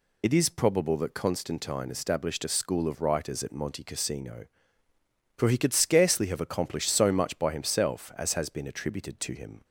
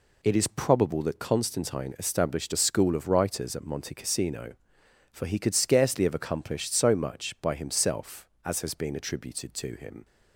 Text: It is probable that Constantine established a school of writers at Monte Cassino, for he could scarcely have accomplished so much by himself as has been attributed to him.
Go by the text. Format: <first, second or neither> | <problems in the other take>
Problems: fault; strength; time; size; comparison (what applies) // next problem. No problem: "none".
second | loses the start of "It"; at 0.2 s; 55 ms